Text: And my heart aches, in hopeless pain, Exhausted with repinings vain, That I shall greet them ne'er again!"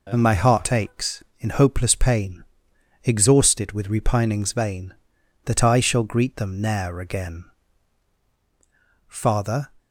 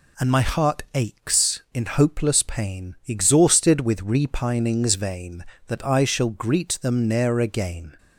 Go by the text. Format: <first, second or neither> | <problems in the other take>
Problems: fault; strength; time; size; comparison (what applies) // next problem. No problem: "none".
second | goes on to say "Father"; noticeable; from 9.0 s on; 0.62 s long